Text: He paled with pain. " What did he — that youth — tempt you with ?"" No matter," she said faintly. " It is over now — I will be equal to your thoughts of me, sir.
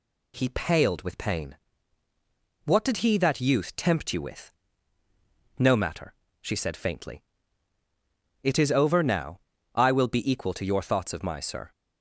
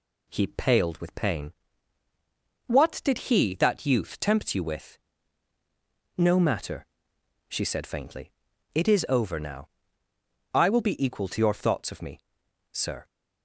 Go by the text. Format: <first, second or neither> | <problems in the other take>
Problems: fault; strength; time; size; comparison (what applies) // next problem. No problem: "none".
second | says "my" for "me"; at 11.2 s